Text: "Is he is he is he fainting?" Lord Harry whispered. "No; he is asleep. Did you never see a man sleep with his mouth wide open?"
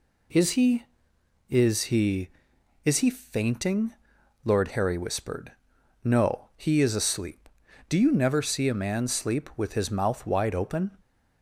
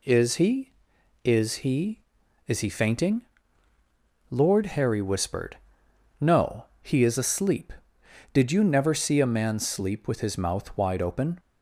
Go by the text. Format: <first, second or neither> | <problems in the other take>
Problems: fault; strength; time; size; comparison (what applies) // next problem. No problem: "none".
second | says "Do" for "Did"; at 7.8 s